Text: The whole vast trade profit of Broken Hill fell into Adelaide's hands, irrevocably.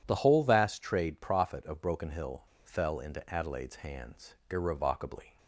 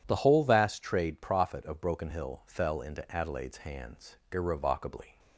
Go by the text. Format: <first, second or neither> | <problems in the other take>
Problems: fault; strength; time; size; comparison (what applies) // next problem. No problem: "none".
second | pauses between "Hill" and "fell"; slight; at 2.4 s; 0.20 s long